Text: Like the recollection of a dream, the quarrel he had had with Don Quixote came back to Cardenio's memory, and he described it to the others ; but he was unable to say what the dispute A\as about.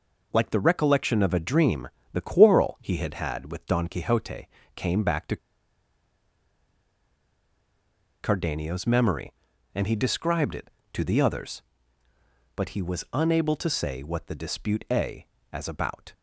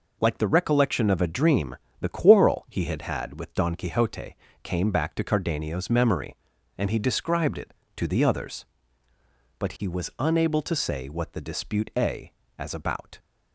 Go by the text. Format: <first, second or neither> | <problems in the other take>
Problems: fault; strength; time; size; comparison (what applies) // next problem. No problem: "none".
second | pauses between "Quixote" and "came"; slight; at 4.4 s; 0.28 s long; slight in the second // pauses between "to" and "Cardenio's"; strong; at 5.3 s; 2.8 s long